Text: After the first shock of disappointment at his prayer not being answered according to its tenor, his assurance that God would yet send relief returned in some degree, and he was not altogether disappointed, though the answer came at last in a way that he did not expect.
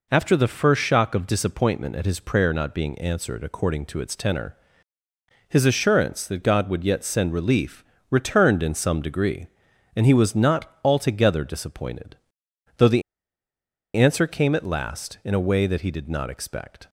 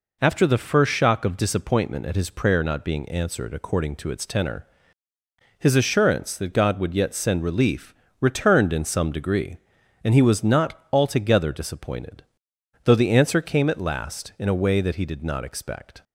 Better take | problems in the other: second | pauses between "relief" and "returned"; slight; at 7.8 s; 0.24 s long; slight in the second // pauses between "the" and "answer"; noticeable; at 13.0 s; 0.92 s long

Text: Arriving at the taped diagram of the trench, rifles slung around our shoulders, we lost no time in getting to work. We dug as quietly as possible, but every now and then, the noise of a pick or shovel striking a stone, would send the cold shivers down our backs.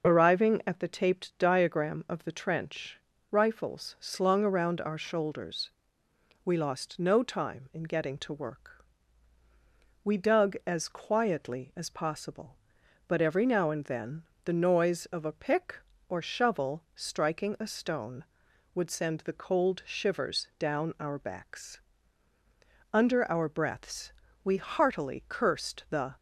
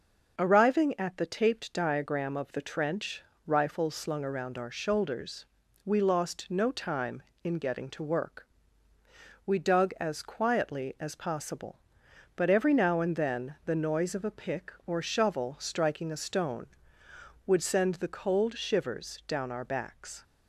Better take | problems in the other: second | starts louder than the rest; noticeable; until 1.1 s; 6 dB; also in the second // goes on to say "Under our breaths we heartily cursed the"; strong; from 22.9 s on; 3.2 s long

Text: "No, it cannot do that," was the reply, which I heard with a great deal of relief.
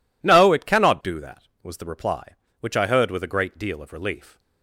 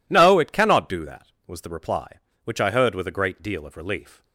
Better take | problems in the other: neither | none

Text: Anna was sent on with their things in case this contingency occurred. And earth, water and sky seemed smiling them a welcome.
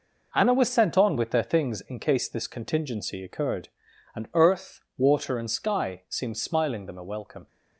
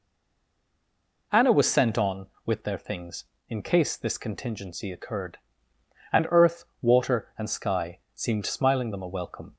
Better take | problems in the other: first | stays silent before the first word; noticeable; until 1.3 s; 1.3 s long

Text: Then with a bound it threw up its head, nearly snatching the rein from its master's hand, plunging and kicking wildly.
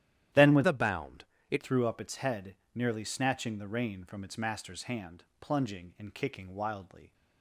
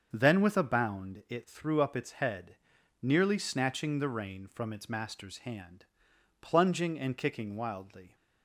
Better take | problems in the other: second | starts louder than the rest; strong; until 1.6 s; 12 dB; also in the second // changes voice from "a" to "it"; from 0.6 to 1.6 s; 1.0 s long // pauses between "bound" and "it"; slight; at 1.2 s; 0.24 s long

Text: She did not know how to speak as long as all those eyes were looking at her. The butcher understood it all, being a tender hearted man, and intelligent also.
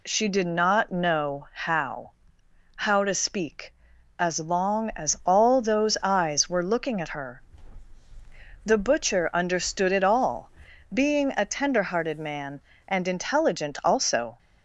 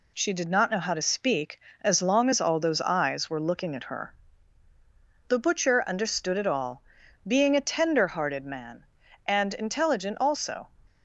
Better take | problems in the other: second | says "how" twice; at 2.7 s

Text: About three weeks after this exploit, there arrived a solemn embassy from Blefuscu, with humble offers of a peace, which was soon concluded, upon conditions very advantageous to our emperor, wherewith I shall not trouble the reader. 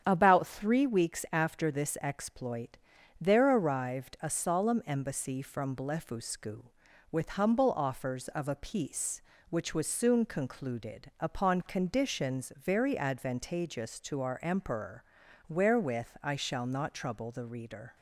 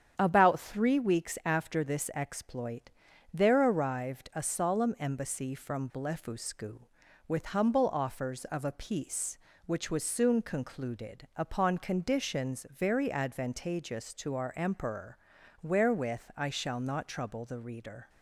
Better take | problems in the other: neither | starts louder than the rest; strong; the same in both

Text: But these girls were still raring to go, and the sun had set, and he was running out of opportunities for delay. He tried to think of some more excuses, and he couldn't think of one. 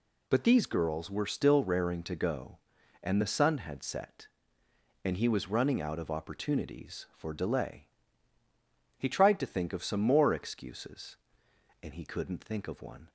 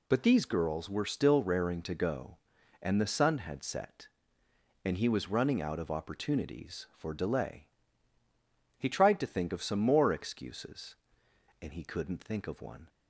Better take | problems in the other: neither | none

